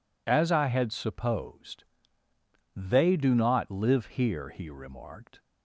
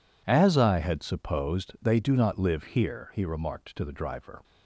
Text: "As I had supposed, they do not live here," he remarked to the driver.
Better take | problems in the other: second | stops before "to the driver"; at 5.3 s

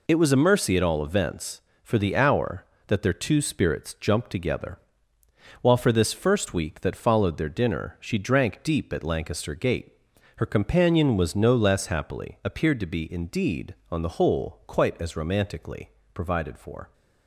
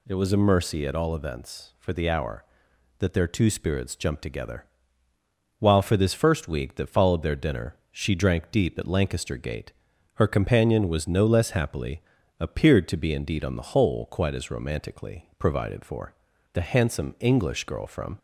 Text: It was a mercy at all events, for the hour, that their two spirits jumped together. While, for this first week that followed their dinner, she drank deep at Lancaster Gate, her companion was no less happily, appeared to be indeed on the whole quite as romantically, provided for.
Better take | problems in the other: first | goes on to say "The handsome English girl from"; from 16.5 s on; 1.6 s long

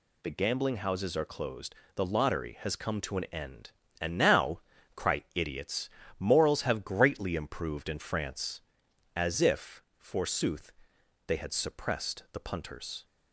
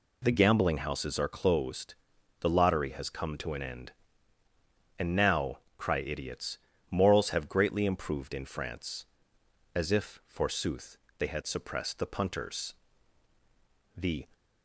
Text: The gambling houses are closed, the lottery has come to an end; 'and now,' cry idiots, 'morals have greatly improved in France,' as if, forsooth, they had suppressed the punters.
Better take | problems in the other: first | goes on to say "The"; slight; from 13.9 s on; 0.30 s long

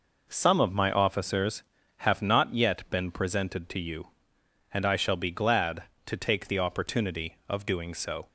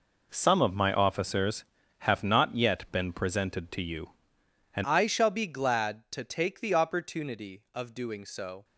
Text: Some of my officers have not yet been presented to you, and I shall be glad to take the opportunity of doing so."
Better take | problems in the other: first | changes voice at "I"; from 4.8 s on; 3.8 s long

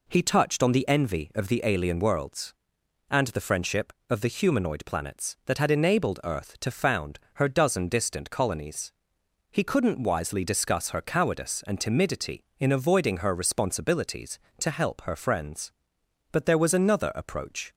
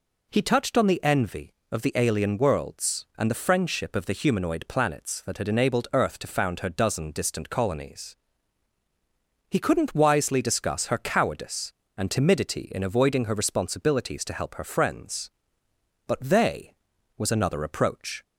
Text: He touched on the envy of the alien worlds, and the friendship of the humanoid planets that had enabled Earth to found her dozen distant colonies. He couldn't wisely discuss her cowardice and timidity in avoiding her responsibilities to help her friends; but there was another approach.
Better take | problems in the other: first | says "they" for "there"; at 16.2 s

